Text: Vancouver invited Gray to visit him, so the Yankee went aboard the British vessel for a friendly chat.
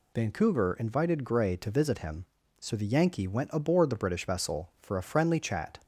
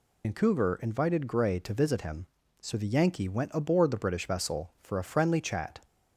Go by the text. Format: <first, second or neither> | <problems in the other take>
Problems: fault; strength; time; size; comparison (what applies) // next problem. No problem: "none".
first | loses the start of "Vancouver"; at 0.2 s; 80 ms